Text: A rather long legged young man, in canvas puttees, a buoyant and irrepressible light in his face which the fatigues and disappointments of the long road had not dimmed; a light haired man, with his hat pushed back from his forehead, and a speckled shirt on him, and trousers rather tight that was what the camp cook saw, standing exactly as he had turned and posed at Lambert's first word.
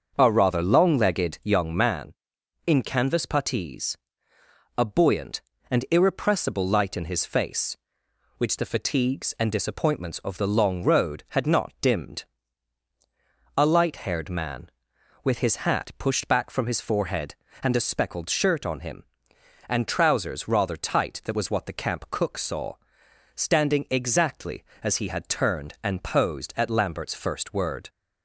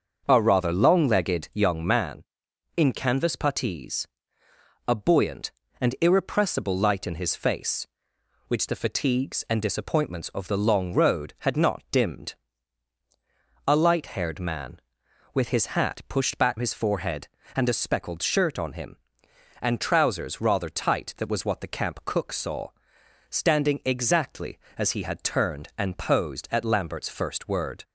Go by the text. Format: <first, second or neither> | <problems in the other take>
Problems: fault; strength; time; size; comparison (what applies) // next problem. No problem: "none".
first | starts louder than the rest; until 1.2 s; 6.5 dB; also in the first // skips "from"; at 16.5 s